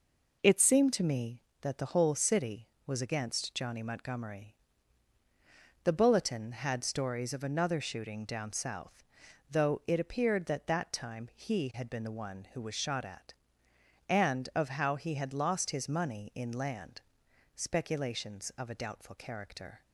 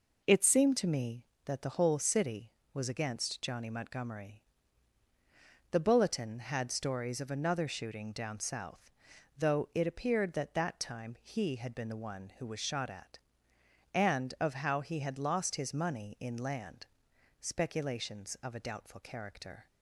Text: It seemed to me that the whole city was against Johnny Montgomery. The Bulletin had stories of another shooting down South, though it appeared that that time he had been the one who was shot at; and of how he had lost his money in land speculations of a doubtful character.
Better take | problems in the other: neither | pauses between "land" and "speculations"; noticeable; the same in both

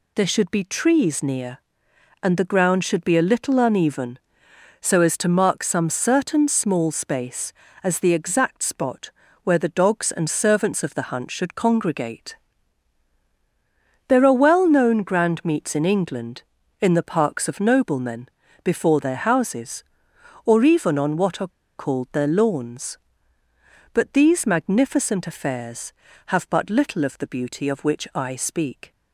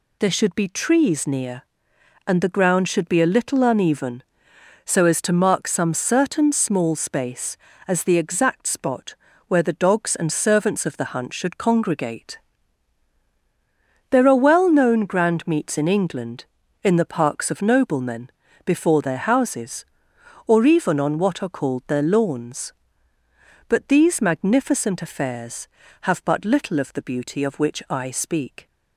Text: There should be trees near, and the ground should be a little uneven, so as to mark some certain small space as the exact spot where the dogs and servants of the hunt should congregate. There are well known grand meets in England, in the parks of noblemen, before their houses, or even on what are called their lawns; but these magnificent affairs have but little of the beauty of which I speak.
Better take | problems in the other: second | pauses between "spot" and "where"; slight; at 9.0 s; 0.34 s long; slight in the second // pauses between "are" and "called"; slight; at 21.4 s; 0.29 s long

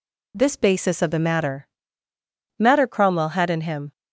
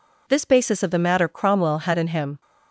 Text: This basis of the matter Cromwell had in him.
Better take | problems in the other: second | says "matter" twice; at 2.5 s

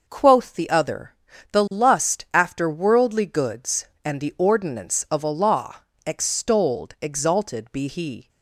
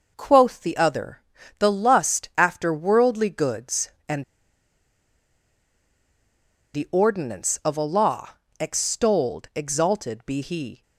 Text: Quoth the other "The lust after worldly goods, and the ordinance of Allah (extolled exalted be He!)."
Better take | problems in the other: first | pauses between "other" and "The"; slight; at 1.2 s; 0.36 s long; slight in the first // pauses between "and" and "the"; strong; at 4.2 s; 2.5 s long

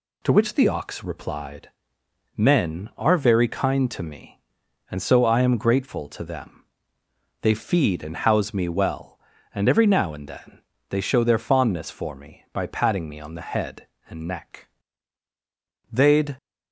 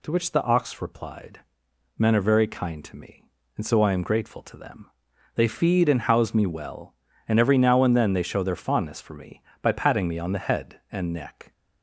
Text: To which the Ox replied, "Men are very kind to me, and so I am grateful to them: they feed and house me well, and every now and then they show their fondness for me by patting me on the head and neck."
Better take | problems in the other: second | pauses between "then" and "they"; slight; at 10.5 s; 0.30 s long // goes on to say "They'd"; slight; from 15.8 s on; 0.46 s long

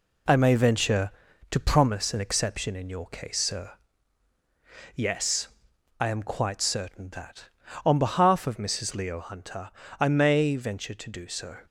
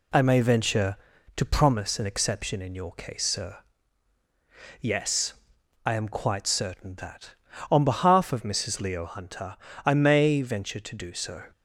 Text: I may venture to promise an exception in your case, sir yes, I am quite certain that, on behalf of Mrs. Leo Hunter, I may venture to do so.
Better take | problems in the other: second | gets quieter; noticeable; throughout; 5.5 dB // pauses between "sir" and "yes"; at 3.7 s; 1.2 s long; also in the second

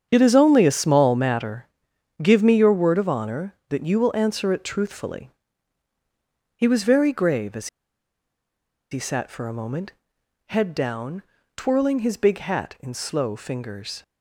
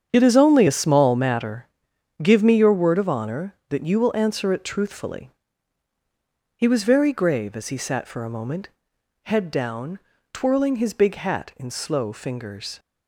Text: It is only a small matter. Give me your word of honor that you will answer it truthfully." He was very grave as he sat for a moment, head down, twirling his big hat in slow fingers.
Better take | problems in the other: second | starts louder than the rest; strong; until 1.1 s; 8 dB; strong in the second // pauses between "as" and "he"; at 7.6 s; 1.2 s long

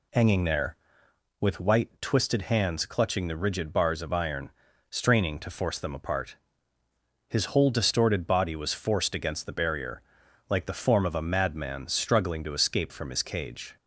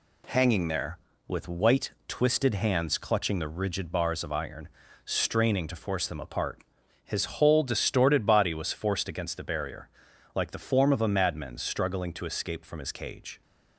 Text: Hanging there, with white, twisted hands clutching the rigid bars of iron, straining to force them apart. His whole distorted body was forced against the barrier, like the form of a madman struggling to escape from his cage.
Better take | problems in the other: neither | none

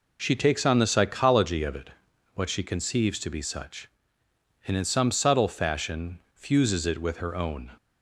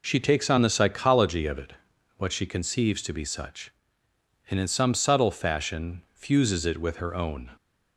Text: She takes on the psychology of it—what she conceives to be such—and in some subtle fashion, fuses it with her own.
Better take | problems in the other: neither | none

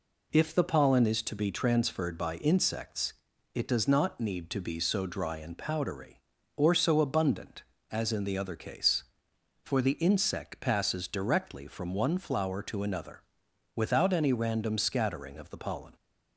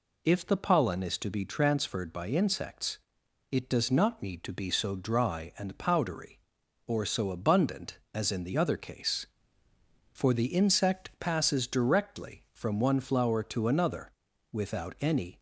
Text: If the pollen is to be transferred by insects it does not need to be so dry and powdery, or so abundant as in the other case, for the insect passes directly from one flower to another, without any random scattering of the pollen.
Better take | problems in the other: first | pauses between "insects" and "it"; noticeable; at 2.9 s; 0.54 s long; also in the first // stops before "random scattering of the pollen"; at 15.3 s

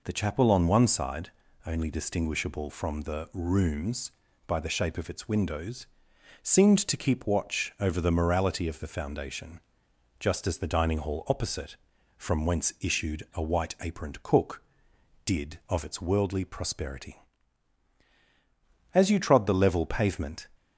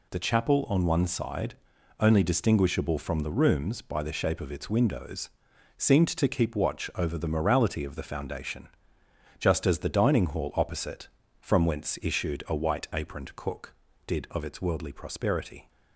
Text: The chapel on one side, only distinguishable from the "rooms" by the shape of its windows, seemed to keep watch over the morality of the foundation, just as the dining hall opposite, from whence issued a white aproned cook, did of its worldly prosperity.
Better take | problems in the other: second | goes on to say "As you trod the level pavement"; from 18.9 s on; 1.5 s long

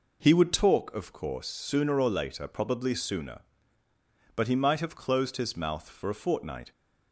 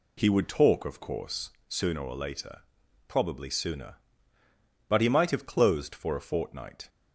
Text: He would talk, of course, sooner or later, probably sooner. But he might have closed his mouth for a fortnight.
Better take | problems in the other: first | skips "his mouth"; at 5.9 s

